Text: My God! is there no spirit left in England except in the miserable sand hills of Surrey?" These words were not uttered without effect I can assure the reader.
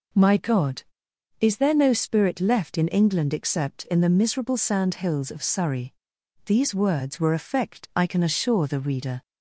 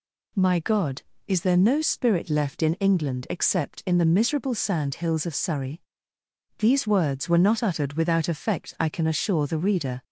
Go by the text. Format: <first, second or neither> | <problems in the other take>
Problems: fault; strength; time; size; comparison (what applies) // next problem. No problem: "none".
second | skips "not uttered without"; at 7.3 s